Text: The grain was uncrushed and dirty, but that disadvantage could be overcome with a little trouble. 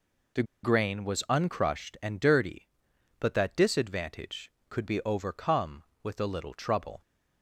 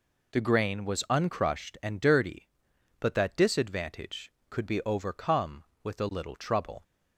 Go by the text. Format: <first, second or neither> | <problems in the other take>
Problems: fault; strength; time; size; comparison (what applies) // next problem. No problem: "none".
second | pauses between "The" and "grain"; slight; at 0.4 s; 0.19 s long